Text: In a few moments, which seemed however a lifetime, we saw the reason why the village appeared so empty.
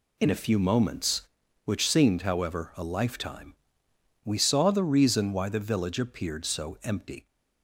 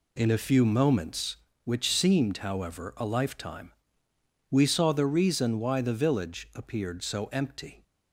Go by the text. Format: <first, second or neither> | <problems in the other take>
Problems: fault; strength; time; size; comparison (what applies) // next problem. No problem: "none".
neither | none